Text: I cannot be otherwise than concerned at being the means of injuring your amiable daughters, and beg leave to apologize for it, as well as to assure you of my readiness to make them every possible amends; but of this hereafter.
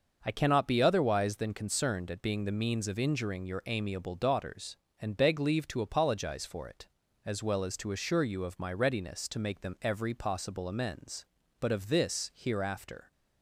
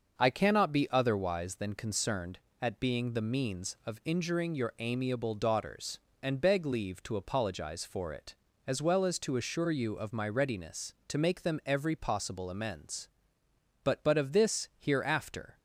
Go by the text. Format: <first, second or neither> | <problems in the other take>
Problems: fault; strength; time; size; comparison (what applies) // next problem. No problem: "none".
first | starts louder than the rest; until 1.2 s; 6.5 dB // says "but" twice; at 14.0 s